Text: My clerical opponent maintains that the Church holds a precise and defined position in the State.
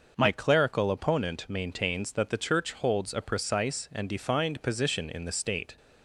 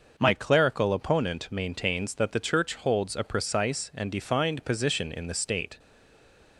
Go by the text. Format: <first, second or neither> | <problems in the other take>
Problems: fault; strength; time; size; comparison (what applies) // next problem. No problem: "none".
first | starts louder than the rest; noticeable; until 1.1 s; 6 dB; noticeable in the first // stays silent after the last word; slight; from 5.7 s on; 0.8 s long